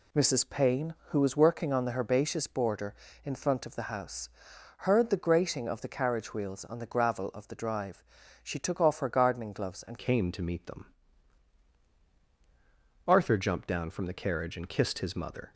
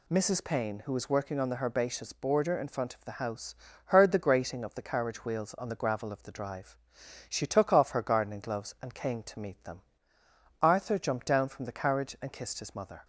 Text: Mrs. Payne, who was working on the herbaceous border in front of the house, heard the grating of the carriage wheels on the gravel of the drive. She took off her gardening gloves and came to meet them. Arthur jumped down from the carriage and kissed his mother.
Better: second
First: changes voice at "came"; from 9.9 s on; 5.6 s long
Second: none

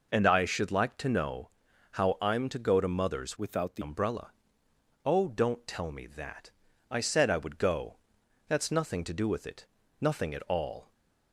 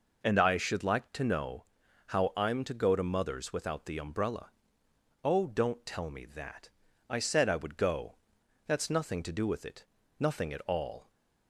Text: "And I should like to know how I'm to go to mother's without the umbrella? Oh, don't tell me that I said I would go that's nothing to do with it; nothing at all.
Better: second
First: pauses between "know" and "how"; at 1.5 s; 0.40 s long // changes voice from "without" to "the"; from 3.3 to 3.8 s; 0.5 s long // pauses between "that" and "I"; at 6.5 s; 0.40 s long // pauses between "go" and "that's"; noticeable; at 7.9 s; 0.50 s long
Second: pauses between "know" and "how"; at 1.6 s; 0.40 s long // pauses between "that" and "I"; at 6.6 s; 0.40 s long // pauses between "go" and "that's"; noticeable; at 8.1 s; 0.50 s long

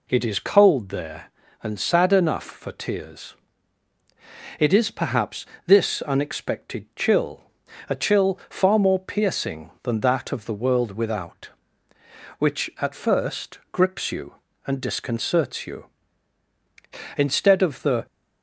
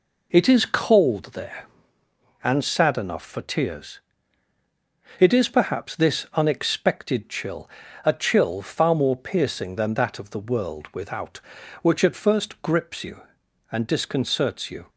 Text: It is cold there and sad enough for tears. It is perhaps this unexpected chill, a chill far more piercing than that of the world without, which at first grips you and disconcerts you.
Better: second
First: pauses between "perhaps" and "this"; slight; at 5.4 s; 0.22 s long // goes on to say "Instead of the"; noticeable; from 17.1 s on; 0.88 s long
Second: none

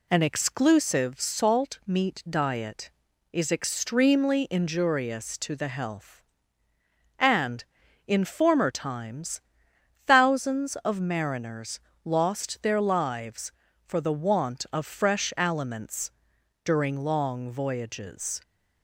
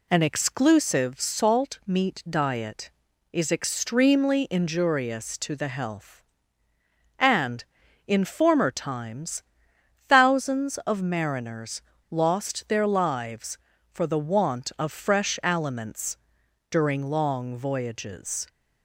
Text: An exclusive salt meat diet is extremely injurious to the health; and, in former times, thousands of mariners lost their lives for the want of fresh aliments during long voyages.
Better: neither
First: pauses between "mariners" and "lost"; slight; at 11.8 s; 0.24 s long // pauses between "aliments" and "during"; noticeable; at 16.1 s; 0.52 s long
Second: pauses between "mariners" and "lost"; slight; at 11.8 s; 0.28 s long // pauses between "aliments" and "during"; noticeable; at 16.1 s; 0.52 s long

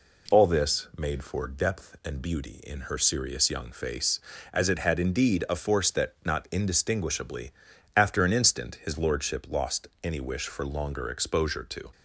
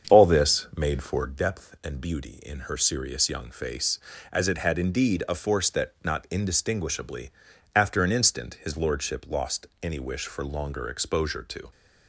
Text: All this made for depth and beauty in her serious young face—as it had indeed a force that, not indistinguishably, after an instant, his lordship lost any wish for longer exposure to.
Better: first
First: pauses between "lost" and "any"; slight; at 9.8 s; 0.16 s long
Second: starts louder than the rest; strong; until 1.4 s; 7.5 dB // pauses between "lost" and "any"; slight; at 9.6 s; 0.16 s long

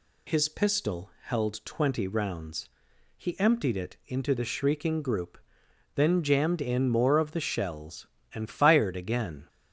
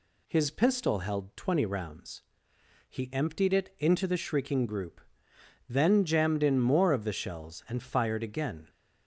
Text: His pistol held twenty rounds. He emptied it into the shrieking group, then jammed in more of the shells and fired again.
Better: neither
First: none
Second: none

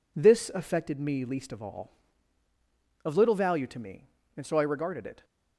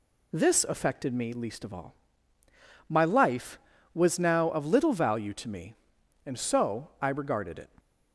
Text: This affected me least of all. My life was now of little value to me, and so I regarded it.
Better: second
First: skips "My life was now"; at 2.4 s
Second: none

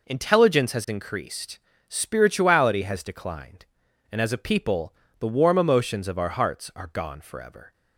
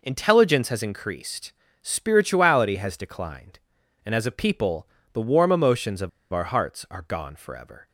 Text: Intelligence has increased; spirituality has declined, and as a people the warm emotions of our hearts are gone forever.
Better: first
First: pauses between "people" and "the"; slight; at 4.9 s; 0.24 s long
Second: pauses between "people" and "the"; slight; at 4.8 s; 0.24 s long // pauses between "of" and "our"; slight; at 6.0 s; 0.23 s long

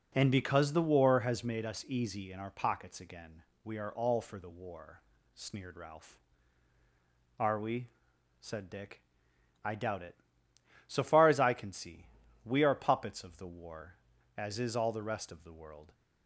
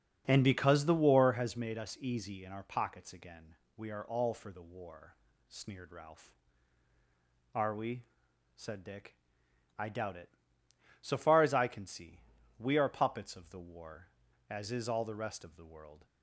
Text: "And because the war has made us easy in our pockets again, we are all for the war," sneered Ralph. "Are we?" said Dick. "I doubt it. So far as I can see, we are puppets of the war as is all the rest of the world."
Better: first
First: none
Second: starts louder than the rest; until 1.4 s; 7 dB

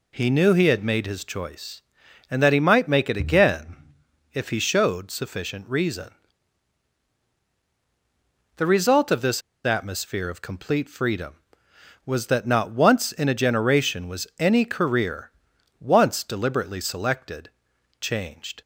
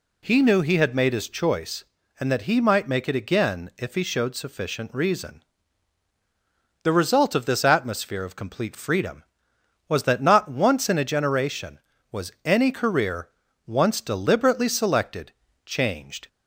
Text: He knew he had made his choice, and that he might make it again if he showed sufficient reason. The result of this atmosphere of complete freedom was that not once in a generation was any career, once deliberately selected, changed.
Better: second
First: pauses between "again" and "if"; noticeable; at 3.7 s; 0.58 s long // pauses between "this" and "atmosphere"; slight; at 9.4 s; 0.24 s long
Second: none

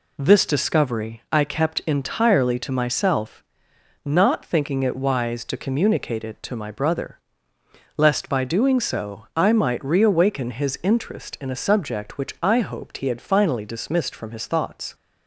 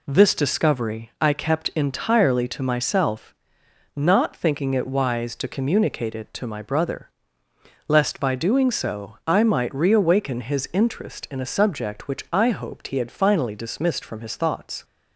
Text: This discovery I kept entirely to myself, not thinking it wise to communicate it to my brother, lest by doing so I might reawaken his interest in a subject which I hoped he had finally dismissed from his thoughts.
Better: neither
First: none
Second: none

